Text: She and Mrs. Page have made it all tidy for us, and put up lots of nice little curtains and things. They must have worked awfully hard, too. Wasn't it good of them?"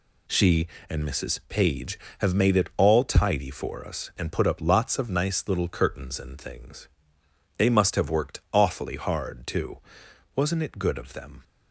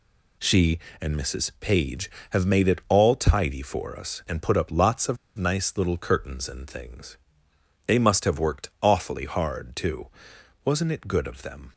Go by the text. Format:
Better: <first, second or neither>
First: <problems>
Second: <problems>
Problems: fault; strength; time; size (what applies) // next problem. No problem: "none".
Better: first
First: none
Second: pauses between "of" and "nice"; slight; at 5.1 s; 0.21 s long